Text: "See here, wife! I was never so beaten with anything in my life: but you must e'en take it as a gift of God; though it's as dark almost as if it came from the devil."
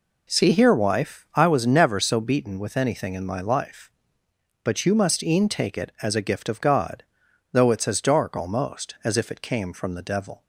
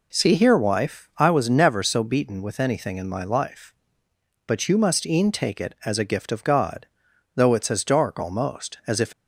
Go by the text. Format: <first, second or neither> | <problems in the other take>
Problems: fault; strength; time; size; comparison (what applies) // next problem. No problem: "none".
first | stops before "it came from the devil"; at 9.1 s